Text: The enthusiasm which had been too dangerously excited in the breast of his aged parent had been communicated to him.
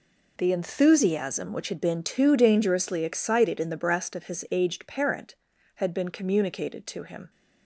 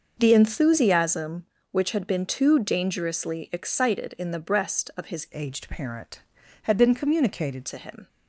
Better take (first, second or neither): first